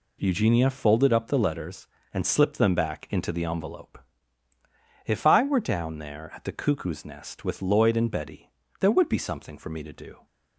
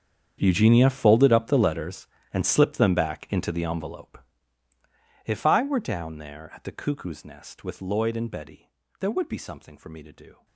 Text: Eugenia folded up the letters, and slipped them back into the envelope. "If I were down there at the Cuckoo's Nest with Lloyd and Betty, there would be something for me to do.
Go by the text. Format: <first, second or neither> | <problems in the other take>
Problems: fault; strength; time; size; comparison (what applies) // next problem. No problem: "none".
first | gets quieter; strong; throughout; 18.5 dB